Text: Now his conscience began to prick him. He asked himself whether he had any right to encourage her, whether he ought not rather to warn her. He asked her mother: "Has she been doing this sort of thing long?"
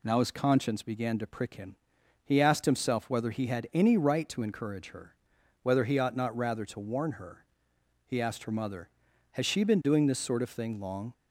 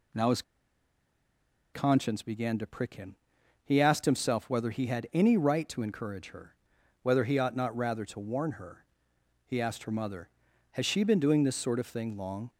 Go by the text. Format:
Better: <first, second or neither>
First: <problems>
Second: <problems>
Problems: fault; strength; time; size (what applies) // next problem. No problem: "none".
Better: first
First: none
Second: pauses between "his" and "conscience"; strong; at 0.4 s; 1.3 s long